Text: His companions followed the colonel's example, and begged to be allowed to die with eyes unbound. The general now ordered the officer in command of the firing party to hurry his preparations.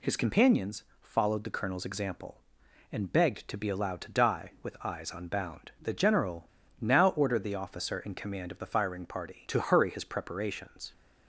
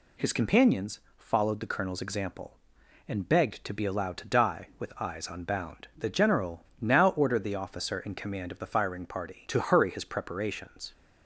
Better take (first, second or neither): second